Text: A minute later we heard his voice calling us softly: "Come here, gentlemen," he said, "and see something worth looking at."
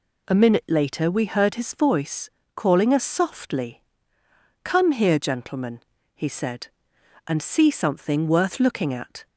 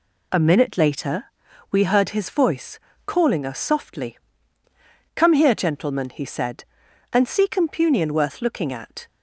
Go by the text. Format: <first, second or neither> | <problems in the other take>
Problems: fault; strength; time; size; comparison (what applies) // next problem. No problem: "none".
first | pauses between "later" and "we"; at 1.2 s; 0.44 s long // pauses between "voice" and "calling"; slight; at 2.8 s; 0.26 s long; slight in the first // says "compunion" for "something"; at 7.4 s